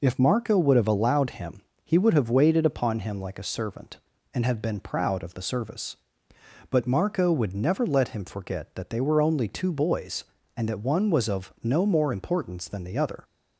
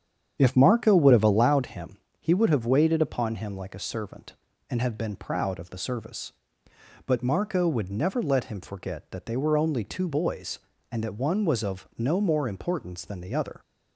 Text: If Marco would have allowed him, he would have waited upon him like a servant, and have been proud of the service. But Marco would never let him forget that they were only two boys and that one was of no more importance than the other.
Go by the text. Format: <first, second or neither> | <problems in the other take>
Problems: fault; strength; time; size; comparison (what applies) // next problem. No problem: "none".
first | starts louder than the rest; strong; until 1.7 s; 8.5 dB